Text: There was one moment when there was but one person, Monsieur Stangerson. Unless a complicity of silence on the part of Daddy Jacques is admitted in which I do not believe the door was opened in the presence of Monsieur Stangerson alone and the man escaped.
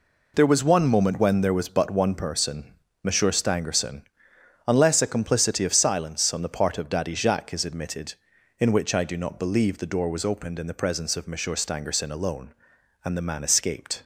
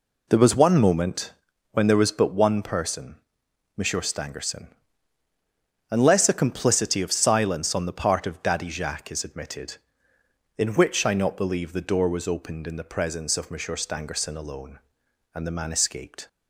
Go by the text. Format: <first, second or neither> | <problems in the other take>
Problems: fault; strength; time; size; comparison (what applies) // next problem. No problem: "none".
first | pauses between "moment" and "when"; at 1.3 s; 0.40 s long // skips "do"; at 11.1 s